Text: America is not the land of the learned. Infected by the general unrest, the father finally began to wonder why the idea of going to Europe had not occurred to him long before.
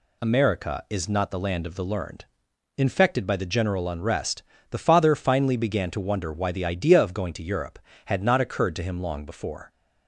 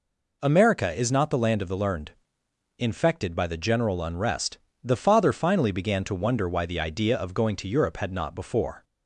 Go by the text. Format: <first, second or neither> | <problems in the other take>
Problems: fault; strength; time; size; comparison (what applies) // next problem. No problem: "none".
first | skips "occurred to him long"; at 8.3 s